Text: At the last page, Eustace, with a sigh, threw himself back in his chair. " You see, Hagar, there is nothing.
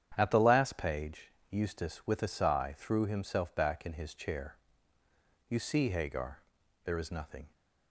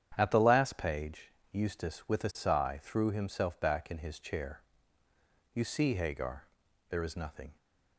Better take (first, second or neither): neither